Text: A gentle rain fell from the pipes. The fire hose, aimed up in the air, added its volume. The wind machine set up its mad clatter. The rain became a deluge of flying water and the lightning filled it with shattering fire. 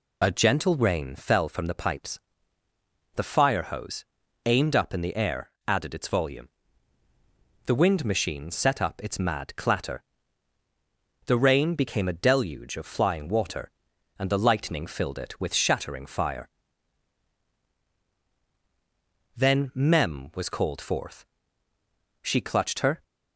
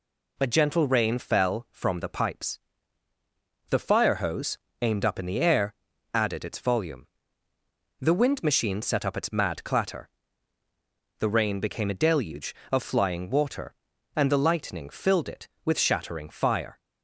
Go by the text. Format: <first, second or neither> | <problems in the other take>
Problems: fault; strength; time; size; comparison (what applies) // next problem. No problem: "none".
second | goes on to say "Then Mem was called forth She clutched her"; strong; from 19.3 s on; 3.6 s long